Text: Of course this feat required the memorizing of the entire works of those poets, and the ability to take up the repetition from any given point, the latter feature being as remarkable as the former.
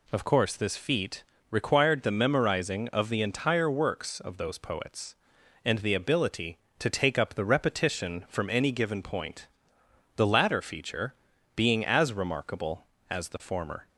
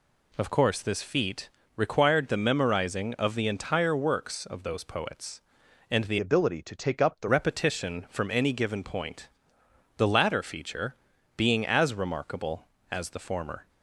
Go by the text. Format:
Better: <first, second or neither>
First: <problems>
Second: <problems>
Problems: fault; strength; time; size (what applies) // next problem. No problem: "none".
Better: first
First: pauses between "feat" and "required"; slight; at 1.2 s; 0.26 s long // pauses between "feature" and "being"; at 11.1 s; 0.42 s long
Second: pauses between "feat" and "required"; slight; at 1.4 s; 0.26 s long // changes voice from "ability" to "the"; from 6.1 to 7.2 s; 1.1 s long // pauses between "feature" and "being"; at 10.9 s; 0.42 s long